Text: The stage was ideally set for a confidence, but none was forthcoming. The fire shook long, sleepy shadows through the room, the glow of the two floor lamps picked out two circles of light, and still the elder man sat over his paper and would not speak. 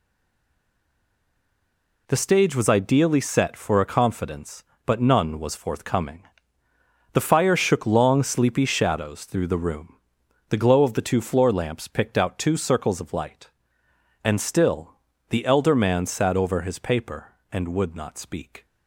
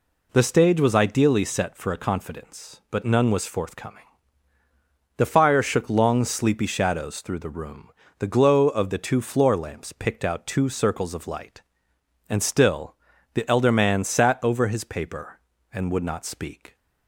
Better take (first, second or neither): second